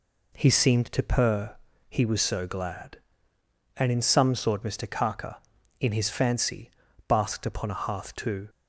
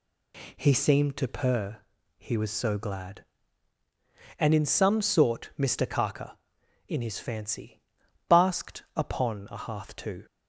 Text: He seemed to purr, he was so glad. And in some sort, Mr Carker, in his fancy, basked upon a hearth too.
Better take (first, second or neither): neither